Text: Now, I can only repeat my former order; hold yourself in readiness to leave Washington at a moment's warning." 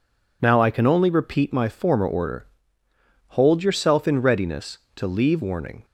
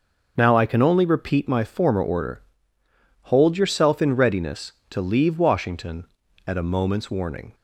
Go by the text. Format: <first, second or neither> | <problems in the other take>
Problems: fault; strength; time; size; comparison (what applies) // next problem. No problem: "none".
second | skips "Washington at a moment's"; at 5.4 s